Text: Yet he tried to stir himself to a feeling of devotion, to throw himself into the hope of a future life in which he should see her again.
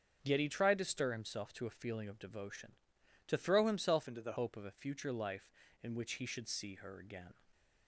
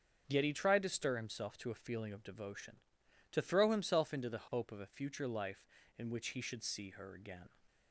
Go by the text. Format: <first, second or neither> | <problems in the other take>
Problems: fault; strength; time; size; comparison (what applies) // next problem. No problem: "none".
second | starts louder than the rest; until 1.2 s; 7 dB; also in the second // changes voice from "into" to "the"; from 4.0 to 4.3 s; 0.3 s long